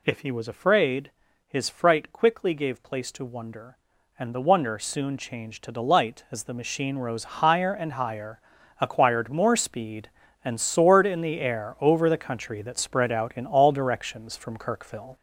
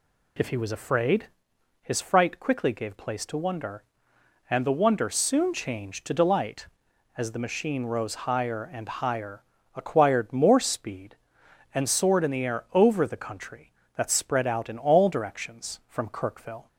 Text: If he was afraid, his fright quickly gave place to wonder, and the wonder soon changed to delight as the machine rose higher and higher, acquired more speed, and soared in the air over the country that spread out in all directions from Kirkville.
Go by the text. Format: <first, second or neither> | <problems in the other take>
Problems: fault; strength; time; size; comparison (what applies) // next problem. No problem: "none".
second | gets louder; noticeable; throughout; 5 dB